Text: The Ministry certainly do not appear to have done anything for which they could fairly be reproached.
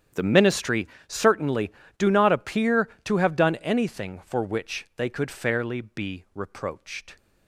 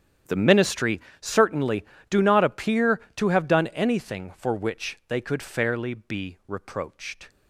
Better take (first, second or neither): neither